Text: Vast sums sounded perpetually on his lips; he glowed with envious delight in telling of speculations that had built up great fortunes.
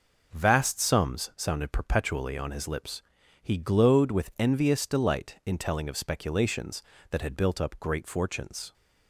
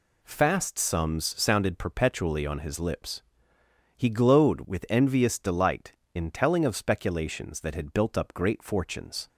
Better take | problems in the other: first | says "Fast" for "Vast"; at 0.2 s

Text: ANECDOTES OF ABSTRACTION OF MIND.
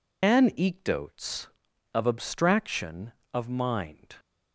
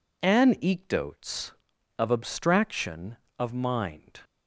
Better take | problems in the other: second | loses the start of "ANECDOTES"; at 0.2 s; 45 ms

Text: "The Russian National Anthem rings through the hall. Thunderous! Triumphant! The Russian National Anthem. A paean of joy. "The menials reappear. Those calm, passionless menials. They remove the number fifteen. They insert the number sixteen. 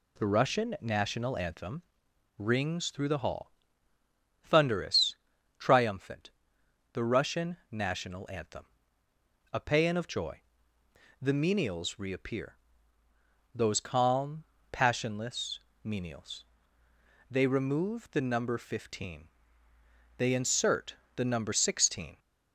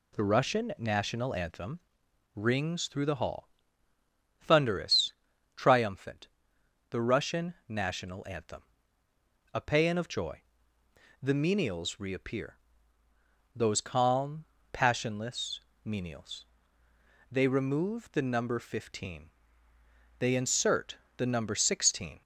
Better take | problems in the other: neither | pauses between "Anthem" and "rings"; noticeable; the same in both // pauses between "passionless" and "menials"; slight; the same in both // pauses between "insert" and "the"; slight; the same in both

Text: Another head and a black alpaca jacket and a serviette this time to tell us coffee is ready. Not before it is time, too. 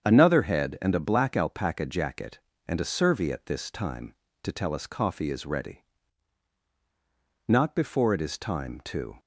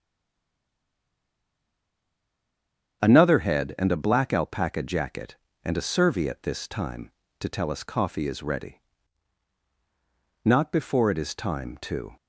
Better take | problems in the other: first | stays silent before the first word; strong; until 3.0 s; 3.0 s long // starts louder than the rest; strong; until 4.0 s; 7.5 dB; strong in the first

